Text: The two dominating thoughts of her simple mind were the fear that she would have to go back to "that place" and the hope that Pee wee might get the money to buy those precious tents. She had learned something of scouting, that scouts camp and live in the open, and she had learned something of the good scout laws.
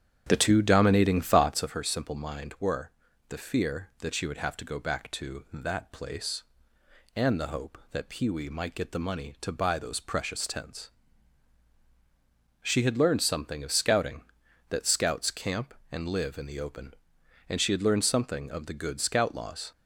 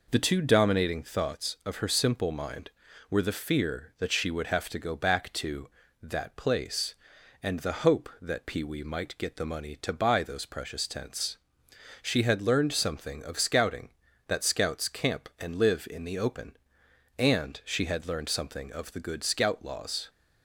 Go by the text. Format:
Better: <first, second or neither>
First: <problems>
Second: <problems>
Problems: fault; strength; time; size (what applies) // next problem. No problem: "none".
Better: second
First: starts louder than the rest; strong; until 1.7 s; 9 dB // pauses between "were" and "the"; at 2.8 s; 0.40 s long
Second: none